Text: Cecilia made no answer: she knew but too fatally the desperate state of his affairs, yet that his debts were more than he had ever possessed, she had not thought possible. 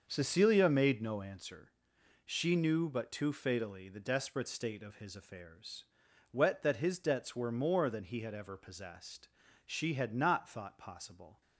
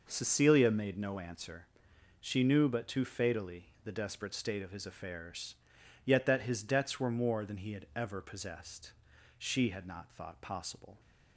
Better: second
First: starts louder than the rest; until 1.0 s; 6.5 dB // says "wet" for "yet"; at 6.3 s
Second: none

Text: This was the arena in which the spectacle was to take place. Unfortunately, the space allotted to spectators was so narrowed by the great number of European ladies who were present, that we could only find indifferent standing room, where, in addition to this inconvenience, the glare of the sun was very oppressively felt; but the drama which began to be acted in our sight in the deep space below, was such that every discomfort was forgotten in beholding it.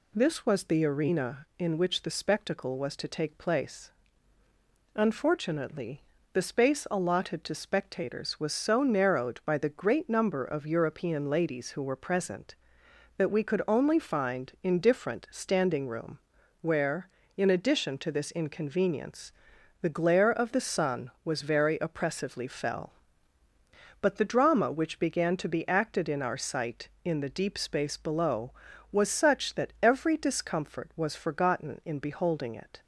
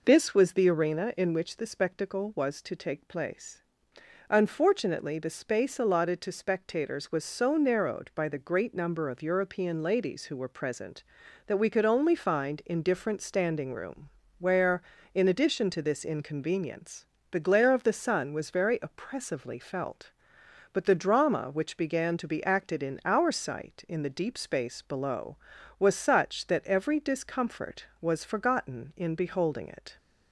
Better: second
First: says "fell" for "felt"; at 22.4 s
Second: none

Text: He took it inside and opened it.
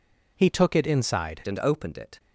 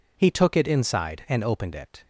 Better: second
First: changes voice at "and"; from 1.4 s on; 0.7 s long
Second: none

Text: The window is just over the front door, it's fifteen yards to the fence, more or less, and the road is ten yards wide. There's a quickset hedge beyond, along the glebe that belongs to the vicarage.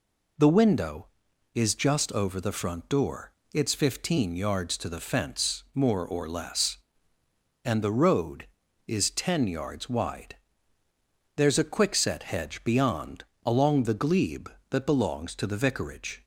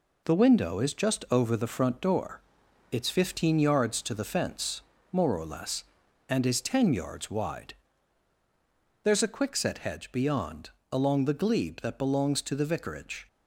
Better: first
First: none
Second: skips "the road"; at 6.4 s

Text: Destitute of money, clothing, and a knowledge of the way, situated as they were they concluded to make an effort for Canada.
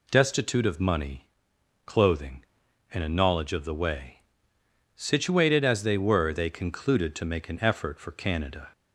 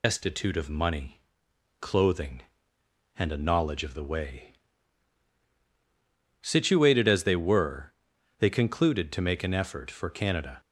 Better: first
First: none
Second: loses the start of "Destitute"; at 0.0 s; 85 ms // pauses between "were" and "they"; at 7.9 s; 0.44 s long

